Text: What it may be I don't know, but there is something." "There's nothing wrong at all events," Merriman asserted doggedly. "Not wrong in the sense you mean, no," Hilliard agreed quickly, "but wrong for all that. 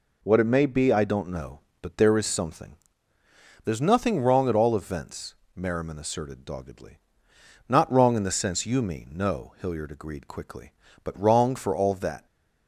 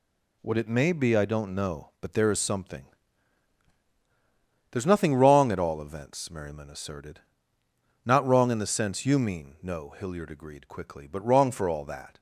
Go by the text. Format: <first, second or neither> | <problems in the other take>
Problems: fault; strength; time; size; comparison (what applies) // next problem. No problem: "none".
first | skips "doggedly"; at 7.6 s